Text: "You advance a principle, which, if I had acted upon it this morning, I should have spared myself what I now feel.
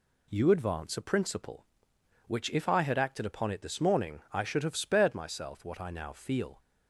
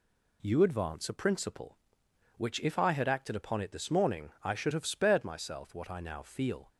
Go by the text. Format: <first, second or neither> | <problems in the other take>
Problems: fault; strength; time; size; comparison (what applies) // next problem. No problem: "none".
neither | none